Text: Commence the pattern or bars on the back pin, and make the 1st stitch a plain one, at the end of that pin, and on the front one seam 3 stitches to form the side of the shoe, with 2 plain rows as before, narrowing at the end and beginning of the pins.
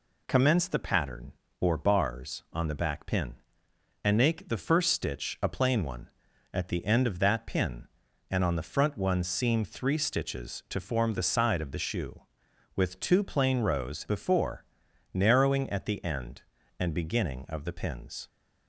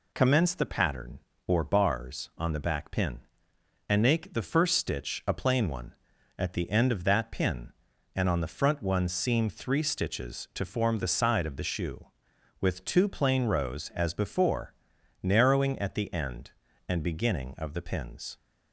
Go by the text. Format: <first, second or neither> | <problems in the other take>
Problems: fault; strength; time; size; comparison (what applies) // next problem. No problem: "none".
second | skips "as"; at 14.0 s